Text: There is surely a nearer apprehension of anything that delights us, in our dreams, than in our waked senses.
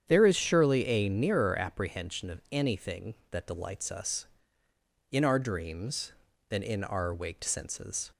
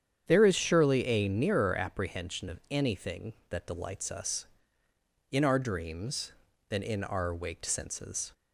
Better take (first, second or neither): neither